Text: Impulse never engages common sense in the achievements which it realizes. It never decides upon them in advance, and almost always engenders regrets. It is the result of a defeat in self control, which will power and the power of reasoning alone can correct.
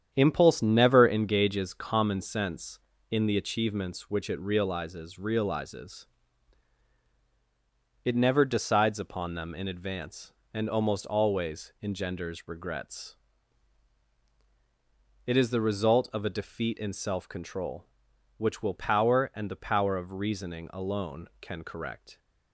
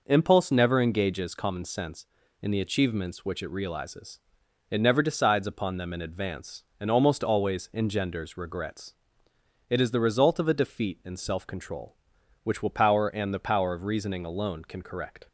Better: second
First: starts louder than the rest; strong; until 1.1 s; 9 dB // says "realizes" twice; at 5.1 s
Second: none

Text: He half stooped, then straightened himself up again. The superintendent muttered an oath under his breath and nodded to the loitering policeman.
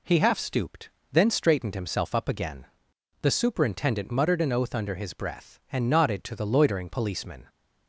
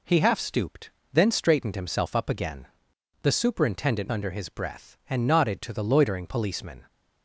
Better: first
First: none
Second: skips "muttered an oath"; at 4.1 s

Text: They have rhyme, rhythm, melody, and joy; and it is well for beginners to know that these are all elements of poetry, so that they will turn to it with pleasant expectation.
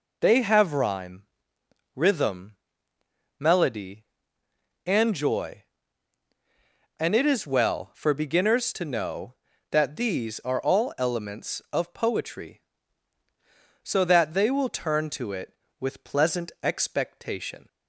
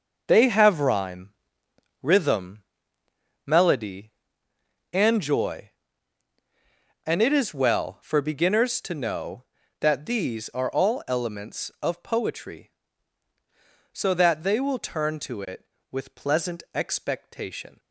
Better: first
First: none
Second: gets quieter; strong; throughout; 10 dB

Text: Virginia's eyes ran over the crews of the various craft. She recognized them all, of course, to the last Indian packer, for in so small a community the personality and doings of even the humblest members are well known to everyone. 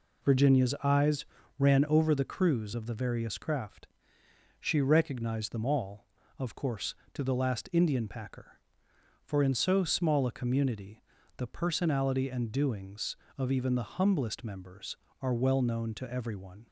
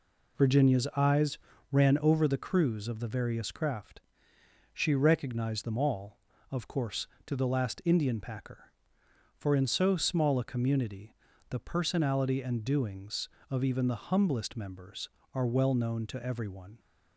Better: neither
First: pauses between "eyes" and "ran"; slight; at 1.2 s; 0.34 s long // pauses between "community" and "the"; slight; at 11.0 s; 0.34 s long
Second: pauses between "eyes" and "ran"; slight; at 1.3 s; 0.34 s long // pauses between "community" and "the"; slight; at 11.1 s; 0.34 s long

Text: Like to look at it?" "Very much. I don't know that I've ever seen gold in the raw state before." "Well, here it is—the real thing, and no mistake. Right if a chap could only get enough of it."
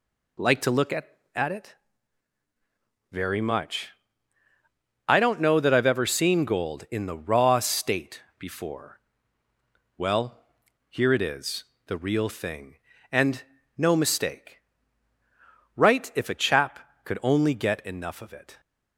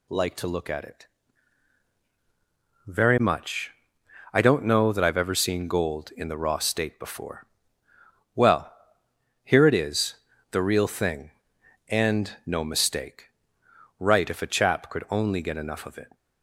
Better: second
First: says "at" twice; at 1.3 s // pauses between "state" and "before"; slight; at 8.2 s; 0.16 s long // pauses between "and" and "no"; slight; at 13.4 s; 0.34 s long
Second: none

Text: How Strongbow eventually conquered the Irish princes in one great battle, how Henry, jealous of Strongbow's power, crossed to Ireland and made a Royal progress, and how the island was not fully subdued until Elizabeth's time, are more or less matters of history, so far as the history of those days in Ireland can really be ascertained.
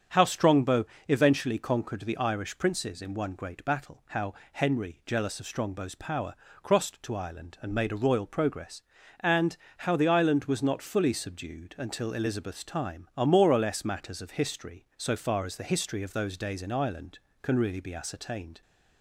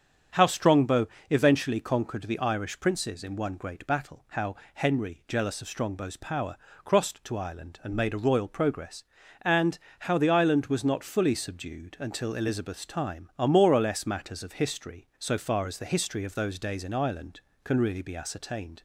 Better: neither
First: starts louder than the rest; strong; until 1.3 s; 7.5 dB // pauses between "Strongbow" and "eventually"; slight; at 0.8 s; 0.20 s long // pauses between "how" and "Henry"; slight; at 4.3 s; 0.20 s long // pauses between "and" and "how"; slight; at 9.5 s; 0.22 s long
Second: starts louder than the rest; strong; until 1.5 s; 7.5 dB // pauses between "Strongbow" and "eventually"; slight; at 1.0 s; 0.20 s long // pauses between "how" and "Henry"; slight; at 4.5 s; 0.20 s long // pauses between "and" and "how"; slight; at 9.7 s; 0.22 s long

